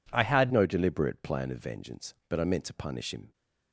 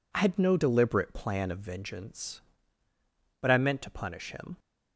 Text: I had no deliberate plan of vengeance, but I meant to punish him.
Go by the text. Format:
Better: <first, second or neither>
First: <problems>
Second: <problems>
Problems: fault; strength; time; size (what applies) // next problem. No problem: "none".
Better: second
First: changes voice at "no"; from 0.5 s on; 2.8 s long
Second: none